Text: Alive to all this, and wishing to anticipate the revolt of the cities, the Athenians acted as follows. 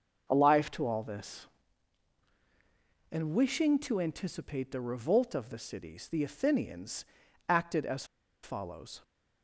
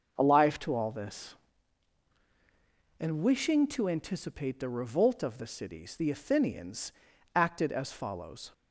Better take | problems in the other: second | starts louder than the rest; noticeable; until 1.3 s; 6 dB; noticeable in the second // pauses between "Athenians" and "acted"; at 7.0 s; 0.42 s long; also in the second // pauses between "as" and "follows"; at 8.0 s; 0.39 s long

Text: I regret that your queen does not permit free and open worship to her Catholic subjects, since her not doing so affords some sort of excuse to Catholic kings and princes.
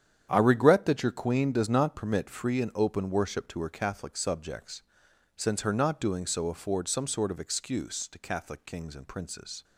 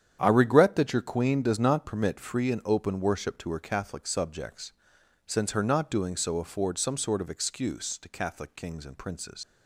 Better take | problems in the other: first | starts louder than the rest; strong; until 1.2 s; 9 dB; strong in the first // leaves "princes" unfinished; at 9.4 s; 100 ms

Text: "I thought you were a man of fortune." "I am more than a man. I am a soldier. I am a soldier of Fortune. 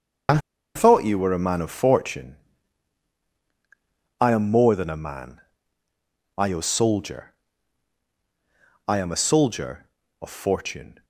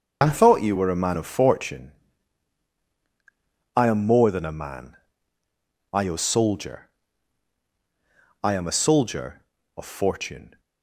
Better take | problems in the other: second | starts louder than the rest; noticeable; until 1.6 s; 6 dB; noticeable in the second // pauses between "I" and "thought"; at 0.3 s; 0.37 s long

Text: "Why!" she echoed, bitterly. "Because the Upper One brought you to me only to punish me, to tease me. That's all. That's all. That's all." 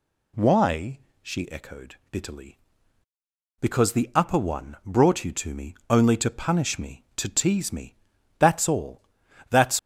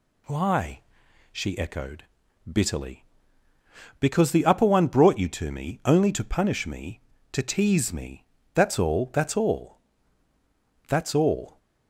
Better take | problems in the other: second | stops before "all That's all"; at 9.7 s

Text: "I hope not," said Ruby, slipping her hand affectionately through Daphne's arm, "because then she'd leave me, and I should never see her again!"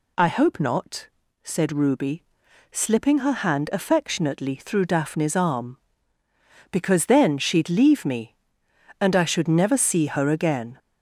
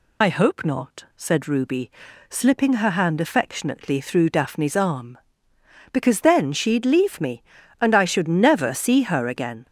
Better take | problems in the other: first | loses the start of "I"; at 0.2 s; 65 ms

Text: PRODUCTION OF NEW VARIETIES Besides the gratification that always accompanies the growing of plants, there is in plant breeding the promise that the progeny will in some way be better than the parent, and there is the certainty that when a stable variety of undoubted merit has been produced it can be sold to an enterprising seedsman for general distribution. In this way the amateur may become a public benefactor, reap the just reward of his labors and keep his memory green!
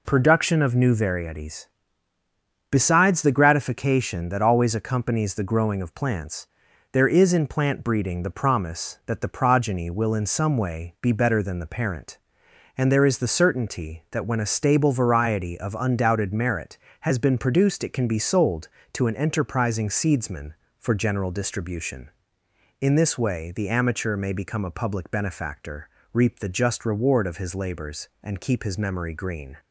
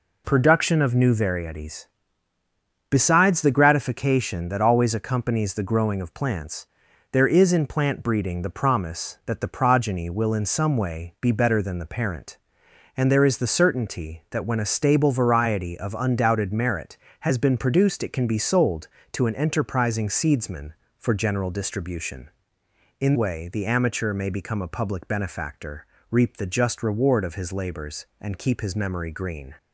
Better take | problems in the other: first | pauses between "VARIETIES" and "Besides"; at 1.8 s; 1.0 s long; also in the first // skips "this"; at 23.1 s

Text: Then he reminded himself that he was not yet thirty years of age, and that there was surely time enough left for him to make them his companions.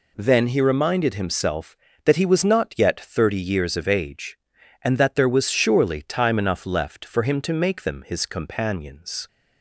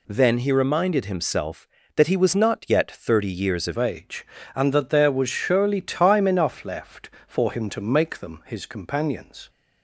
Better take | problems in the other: first | changes voice at "age"; from 3.7 s on; 5.7 s long

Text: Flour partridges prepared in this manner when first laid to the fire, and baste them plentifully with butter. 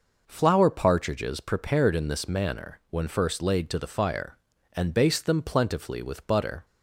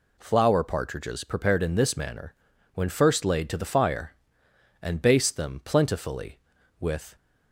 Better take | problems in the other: first | pauses between "manner" and "when"; at 2.3 s; 0.40 s long // stops before "butter"; at 7.1 s

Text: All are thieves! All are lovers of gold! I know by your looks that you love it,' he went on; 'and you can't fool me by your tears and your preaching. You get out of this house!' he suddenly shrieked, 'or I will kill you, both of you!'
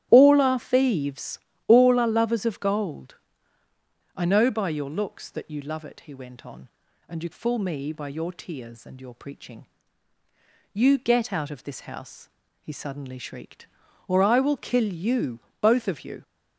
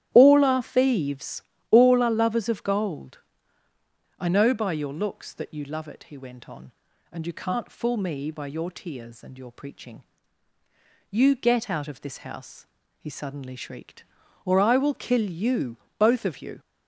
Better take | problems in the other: second | starts louder than the rest; strong; until 1.1 s; 12 dB; strong in the second // skips "can't"; at 7.3 s

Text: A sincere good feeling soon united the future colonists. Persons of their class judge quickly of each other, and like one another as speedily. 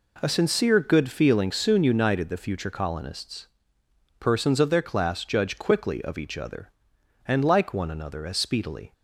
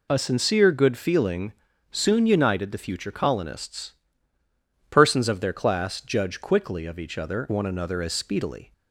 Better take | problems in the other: first | pauses between "feeling" and "soon"; slight; at 1.5 s; 0.36 s long // skips "and like"; at 7.4 s

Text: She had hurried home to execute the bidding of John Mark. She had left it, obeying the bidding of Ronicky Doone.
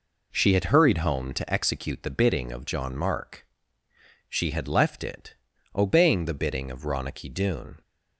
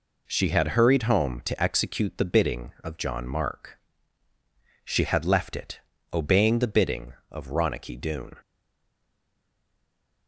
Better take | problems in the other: first | stays silent after the last word; noticeable; from 8.4 s on; 1.8 s long

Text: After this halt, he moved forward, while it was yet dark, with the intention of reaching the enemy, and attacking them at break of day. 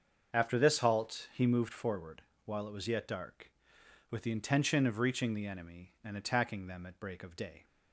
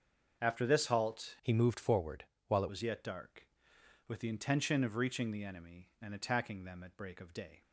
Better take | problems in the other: first | starts louder than the rest; until 1.4 s; 6.5 dB; also in the first // changes voice from "he" to "it"; from 1.4 to 2.6 s; 1.2 s long

